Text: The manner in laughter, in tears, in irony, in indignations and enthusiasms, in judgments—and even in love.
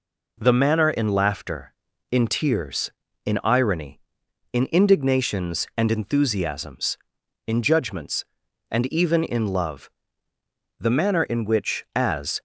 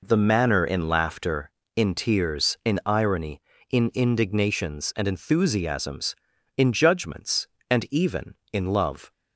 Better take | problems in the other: second | goes on to say "The manner in which as"; from 10.7 s on; 1.6 s long

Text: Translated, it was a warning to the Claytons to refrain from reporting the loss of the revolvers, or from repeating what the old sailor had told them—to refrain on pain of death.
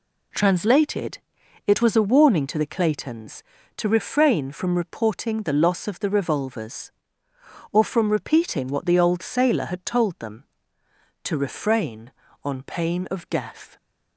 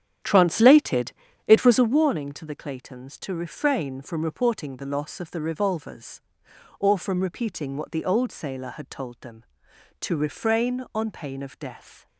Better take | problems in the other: first | starts louder than the rest; strong; until 2.0 s; 9.5 dB

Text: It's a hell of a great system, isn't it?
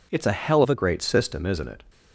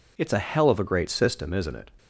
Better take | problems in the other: second | changes voice from "of" to "a"; from 0.6 to 0.7 s; 0.1 s long

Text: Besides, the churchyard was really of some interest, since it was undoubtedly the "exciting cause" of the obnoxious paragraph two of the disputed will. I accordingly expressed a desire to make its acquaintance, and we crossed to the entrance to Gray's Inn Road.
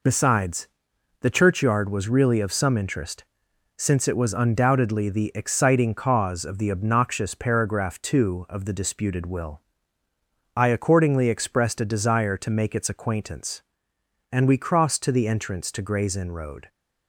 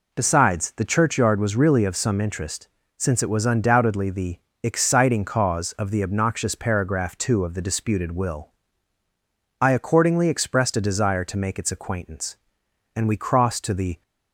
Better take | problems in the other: first | pauses between "the" and "exciting"; slight; at 4.3 s; 0.22 s long // stops before "entrance to Gray's Inn Road"; at 14.0 s

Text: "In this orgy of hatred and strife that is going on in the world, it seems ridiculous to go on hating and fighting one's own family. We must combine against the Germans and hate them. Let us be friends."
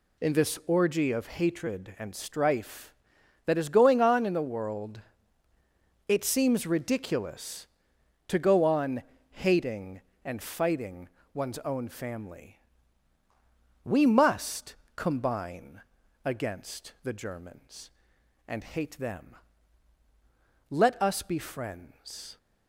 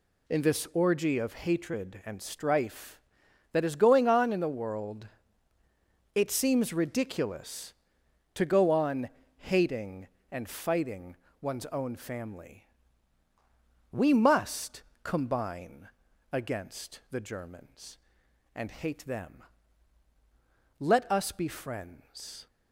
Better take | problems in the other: neither | pauses between "on" and "hating"; slight; the same in both // pauses between "fighting" and "one's"; slight; the same in both // pauses between "must" and "combine"; slight; the same in both // pauses between "combine" and "against"; the same in both

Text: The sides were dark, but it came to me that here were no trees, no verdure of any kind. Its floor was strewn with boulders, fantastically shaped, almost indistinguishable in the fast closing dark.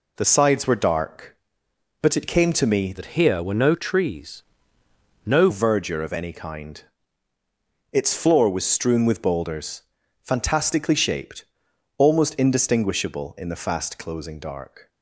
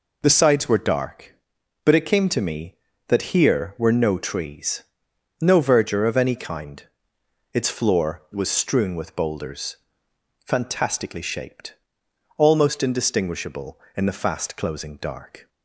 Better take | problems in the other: second | changes voice from "that" to "no"; from 2.9 to 5.4 s; 2.5 s long

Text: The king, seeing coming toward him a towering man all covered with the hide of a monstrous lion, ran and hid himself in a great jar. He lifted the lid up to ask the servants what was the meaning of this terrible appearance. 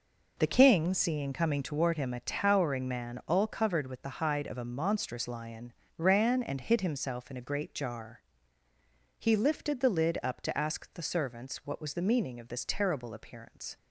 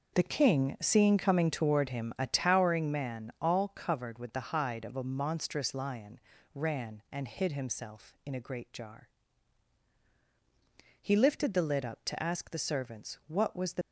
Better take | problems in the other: first | stops before "meaning of this terrible appearance"; at 13.8 s

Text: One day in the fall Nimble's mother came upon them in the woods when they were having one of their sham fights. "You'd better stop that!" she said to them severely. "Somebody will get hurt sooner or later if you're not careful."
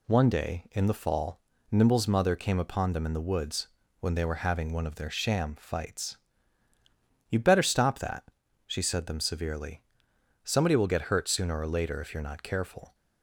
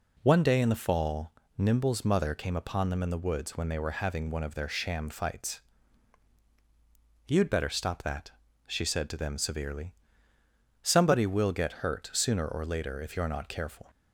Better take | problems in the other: second | pauses between "fall" and "Nimble's"; slight; at 1.4 s; 0.30 s long; slight in the second // pauses between "woods" and "when"; slight; at 3.6 s; 0.32 s long // skips "to"; at 9.0 s

